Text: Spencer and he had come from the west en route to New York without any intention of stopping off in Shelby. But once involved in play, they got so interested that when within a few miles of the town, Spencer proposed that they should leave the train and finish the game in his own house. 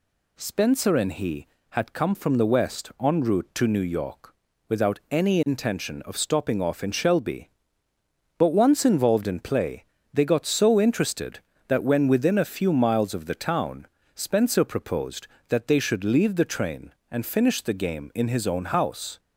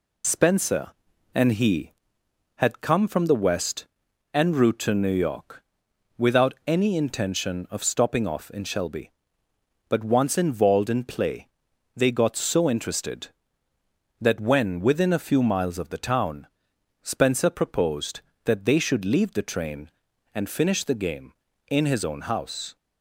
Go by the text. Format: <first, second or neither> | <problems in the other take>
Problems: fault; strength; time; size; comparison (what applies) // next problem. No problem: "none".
first | loses the start of "Spencer"; at 0.2 s; 45 ms // pauses between "west" and "en"; noticeable; at 3.8 s; 0.48 s long // pauses between "York" and "without"; noticeable; at 5.6 s; 0.56 s long; slight in the first